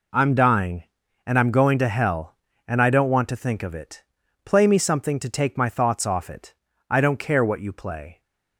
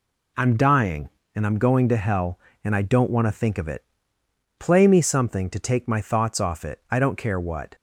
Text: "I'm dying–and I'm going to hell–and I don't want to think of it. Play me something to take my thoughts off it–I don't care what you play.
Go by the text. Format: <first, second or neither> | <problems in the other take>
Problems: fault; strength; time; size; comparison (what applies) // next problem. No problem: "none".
first | stops before "you play"; at 7.7 s